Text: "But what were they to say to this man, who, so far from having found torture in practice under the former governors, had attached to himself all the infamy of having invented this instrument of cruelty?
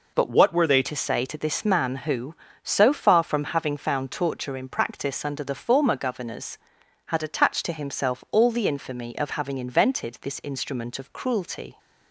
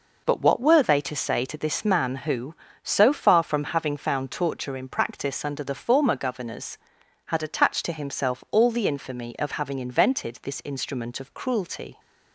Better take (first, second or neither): second